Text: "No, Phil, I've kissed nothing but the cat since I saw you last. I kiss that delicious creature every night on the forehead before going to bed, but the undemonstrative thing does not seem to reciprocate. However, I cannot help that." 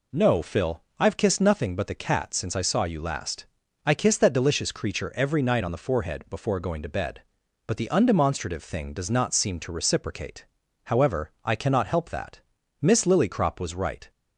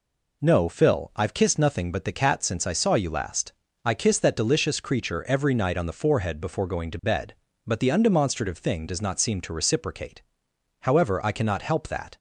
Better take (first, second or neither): second